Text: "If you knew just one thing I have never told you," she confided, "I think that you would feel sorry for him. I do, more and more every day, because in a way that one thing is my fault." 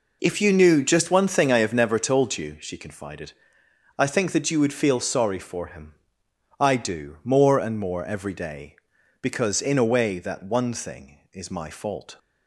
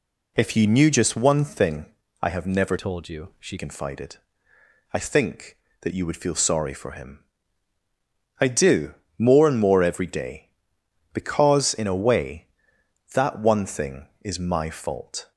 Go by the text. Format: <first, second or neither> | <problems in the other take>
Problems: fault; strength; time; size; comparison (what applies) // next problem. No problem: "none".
first | pauses between "thing" and "I"; slight; at 1.8 s; 0.34 s long // changes voice from "told" to "she"; from 2.7 to 3.5 s; 0.8 s long